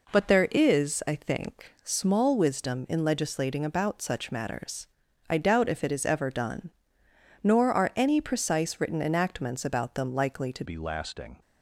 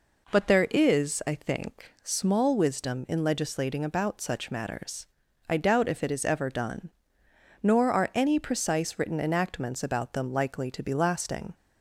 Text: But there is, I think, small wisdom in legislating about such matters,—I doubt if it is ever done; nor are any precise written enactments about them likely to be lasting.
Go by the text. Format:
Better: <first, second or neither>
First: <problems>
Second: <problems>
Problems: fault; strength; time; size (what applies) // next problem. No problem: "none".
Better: second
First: changes voice at "be"; from 10.6 s on; 0.8 s long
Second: none